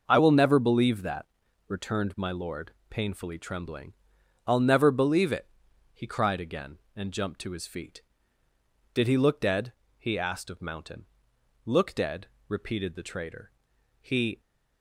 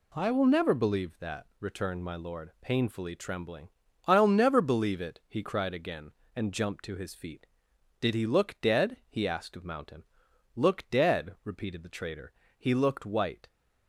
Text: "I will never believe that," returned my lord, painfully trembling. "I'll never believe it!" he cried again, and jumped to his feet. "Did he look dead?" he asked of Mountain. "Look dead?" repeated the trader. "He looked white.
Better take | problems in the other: second | stops before "looked white"; at 14.3 s

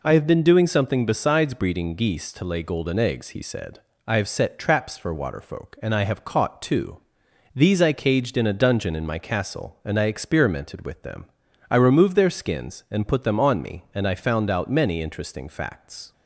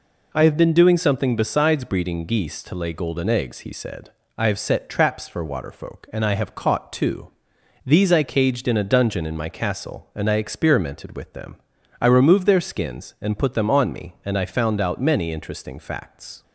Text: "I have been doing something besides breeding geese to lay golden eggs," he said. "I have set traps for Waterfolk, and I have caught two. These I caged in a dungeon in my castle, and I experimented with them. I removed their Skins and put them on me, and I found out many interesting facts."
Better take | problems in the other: neither | none

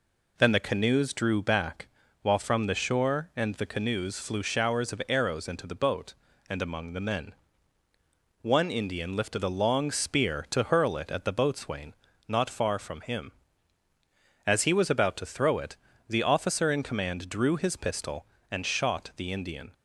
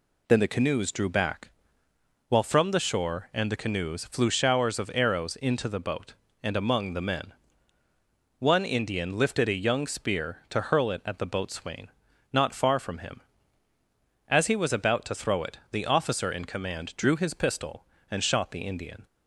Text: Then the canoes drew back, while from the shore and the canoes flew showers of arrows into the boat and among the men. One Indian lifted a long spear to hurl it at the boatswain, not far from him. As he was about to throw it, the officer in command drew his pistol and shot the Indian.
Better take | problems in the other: first | says "young" for "long"; at 9.6 s

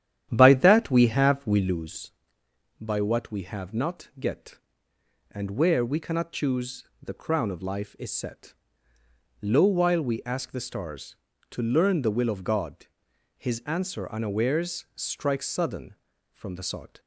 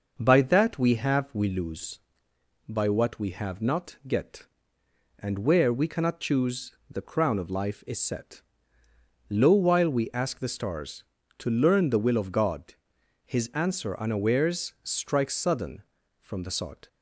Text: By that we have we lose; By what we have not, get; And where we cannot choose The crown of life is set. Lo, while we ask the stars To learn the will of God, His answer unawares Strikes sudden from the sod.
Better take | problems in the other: second | starts louder than the rest; strong; until 1.9 s; 10.5 dB // pauses between "choose" and "The"; slight; at 6.8 s; 0.18 s long; slight in the second

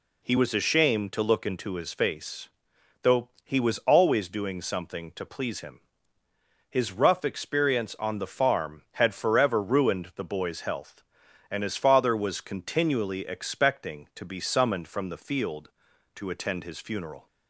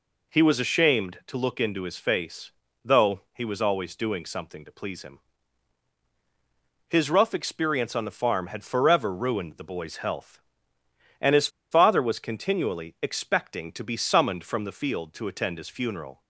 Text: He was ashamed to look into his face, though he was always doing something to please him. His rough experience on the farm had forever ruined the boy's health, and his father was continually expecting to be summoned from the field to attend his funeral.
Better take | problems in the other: first | pauses between "his" and "father"; slight; at 11.4 s; 0.23 s long

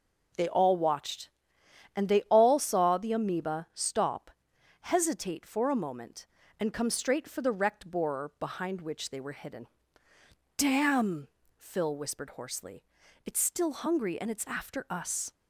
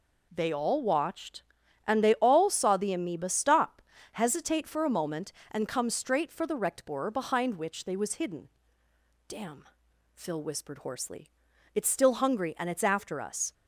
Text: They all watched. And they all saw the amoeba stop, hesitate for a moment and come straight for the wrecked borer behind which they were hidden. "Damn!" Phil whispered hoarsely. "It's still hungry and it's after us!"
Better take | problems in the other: first | says "was" for "were"; at 7.9 s

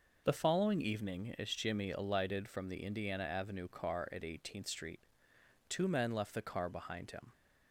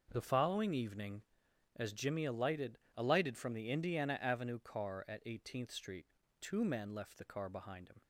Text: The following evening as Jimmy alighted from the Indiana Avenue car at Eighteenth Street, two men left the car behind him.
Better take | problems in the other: first | starts louder than the rest; noticeable; until 1.1 s; 6 dB // says "alighted" twice; at 2.9 s

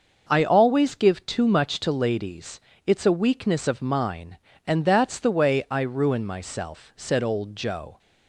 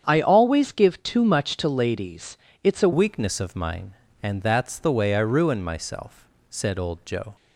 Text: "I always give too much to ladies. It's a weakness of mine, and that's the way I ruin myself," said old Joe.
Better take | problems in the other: first | starts louder than the rest; strong; until 1.0 s; 8 dB; noticeable in the first // changes voice at "weakness"; from 2.9 s on; 4.4 s long

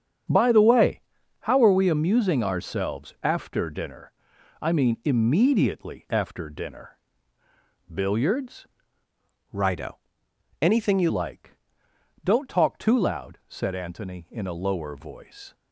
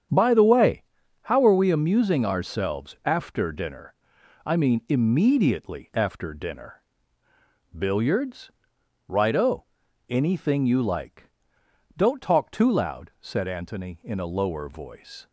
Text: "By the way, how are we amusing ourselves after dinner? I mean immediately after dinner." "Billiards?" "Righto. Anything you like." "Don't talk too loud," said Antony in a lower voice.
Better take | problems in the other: second | starts louder than the rest; strong; until 1.6 s; 8 dB; strong in the second // changes voice from "Righto" to "you"; from 9.5 to 11.0 s; 1.5 s long

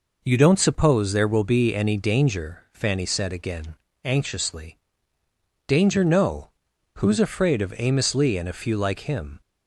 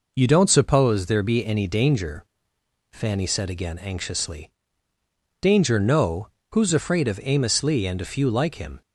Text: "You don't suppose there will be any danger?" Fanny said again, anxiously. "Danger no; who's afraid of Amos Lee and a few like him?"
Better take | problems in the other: first | skips "will"; at 1.2 s

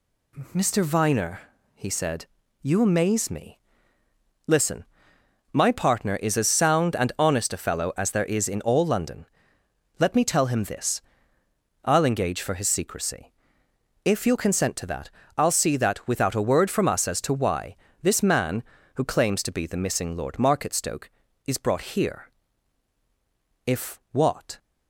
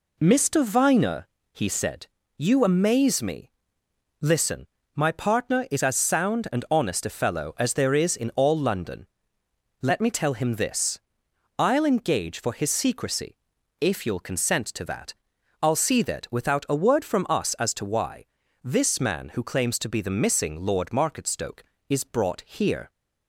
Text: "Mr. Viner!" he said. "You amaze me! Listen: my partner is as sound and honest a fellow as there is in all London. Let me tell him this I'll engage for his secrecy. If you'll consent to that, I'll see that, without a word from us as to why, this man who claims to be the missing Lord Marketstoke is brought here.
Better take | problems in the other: second | pauses between "this" and "I'll"; noticeable; at 11.0 s; 0.84 s long; noticeable in the second // goes on to say "If what"; noticeable; from 23.6 s on; 0.92 s long

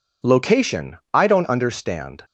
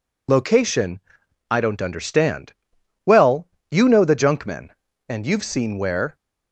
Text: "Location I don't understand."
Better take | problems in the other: first | pauses between "Location" and "I"; noticeable; at 0.9 s; 0.50 s long // goes on to say "Well you know the junkmen and you've seen where"; strong; from 3.0 s on; 3.1 s long

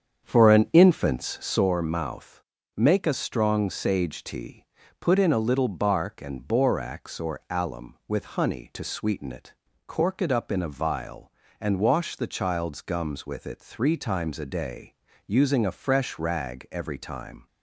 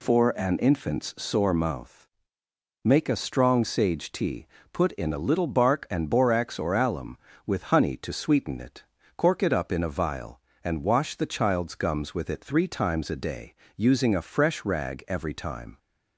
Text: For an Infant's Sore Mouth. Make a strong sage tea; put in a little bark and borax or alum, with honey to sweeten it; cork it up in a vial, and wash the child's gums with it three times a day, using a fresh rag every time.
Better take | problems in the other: second | starts louder than the rest; strong; until 1.7 s; 7.5 dB

